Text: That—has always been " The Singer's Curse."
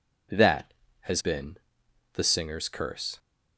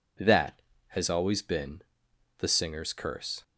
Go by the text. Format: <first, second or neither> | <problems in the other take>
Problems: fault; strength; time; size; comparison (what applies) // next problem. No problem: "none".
second | skips "always"; at 1.2 s